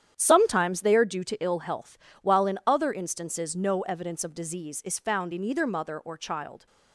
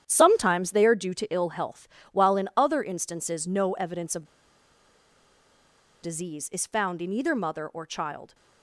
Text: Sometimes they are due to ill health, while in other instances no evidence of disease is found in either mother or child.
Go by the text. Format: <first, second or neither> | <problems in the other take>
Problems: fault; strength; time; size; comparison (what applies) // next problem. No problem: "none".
first | starts louder than the rest; strong; until 1.0 s; 10 dB; strong in the first // pauses between "of" and "disease"; strong; at 4.2 s; 1.7 s long